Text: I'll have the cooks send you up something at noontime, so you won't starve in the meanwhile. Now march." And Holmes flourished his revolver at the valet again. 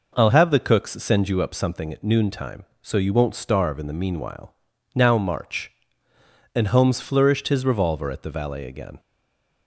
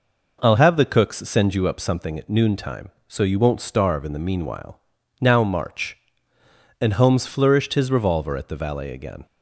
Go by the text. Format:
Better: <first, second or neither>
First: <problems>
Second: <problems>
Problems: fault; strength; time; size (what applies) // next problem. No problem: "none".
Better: second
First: stays silent after the last word; slight; from 8.9 s on; 0.7 s long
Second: none